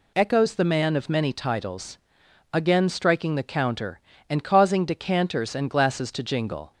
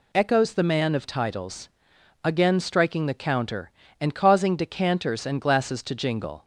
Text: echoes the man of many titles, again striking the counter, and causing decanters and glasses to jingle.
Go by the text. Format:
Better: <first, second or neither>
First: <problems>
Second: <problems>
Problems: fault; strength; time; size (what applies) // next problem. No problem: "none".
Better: first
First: none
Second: skips "many"; at 1.0 s